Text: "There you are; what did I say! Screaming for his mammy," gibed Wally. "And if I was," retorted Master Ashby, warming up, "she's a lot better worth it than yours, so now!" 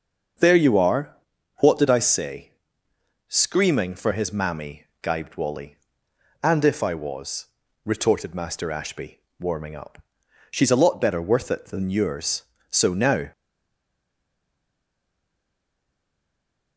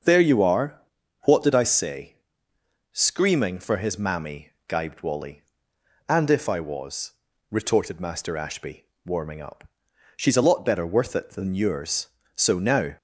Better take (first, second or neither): second